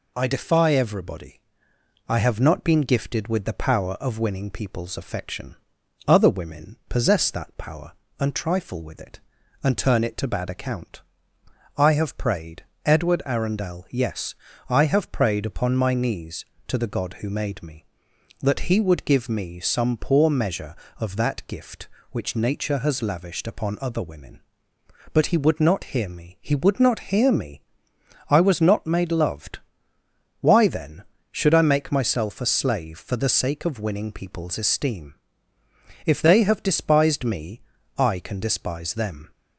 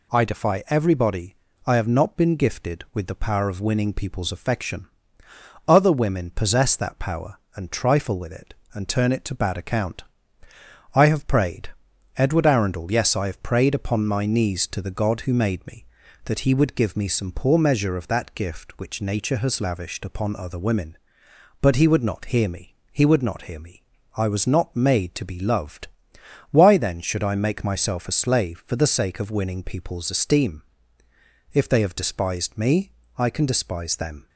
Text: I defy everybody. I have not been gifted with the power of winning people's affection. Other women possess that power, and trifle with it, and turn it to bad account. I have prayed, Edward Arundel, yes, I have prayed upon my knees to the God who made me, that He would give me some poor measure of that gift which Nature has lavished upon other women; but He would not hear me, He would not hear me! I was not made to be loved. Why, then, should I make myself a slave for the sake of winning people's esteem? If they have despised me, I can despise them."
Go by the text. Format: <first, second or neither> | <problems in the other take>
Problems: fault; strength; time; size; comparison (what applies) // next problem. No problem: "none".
second | skips "to be"; at 29.1 s